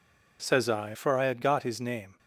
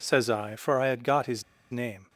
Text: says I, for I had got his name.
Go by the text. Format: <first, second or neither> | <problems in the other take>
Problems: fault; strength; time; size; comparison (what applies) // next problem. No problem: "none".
first | pauses between "his" and "name"; slight; at 1.4 s; 0.28 s long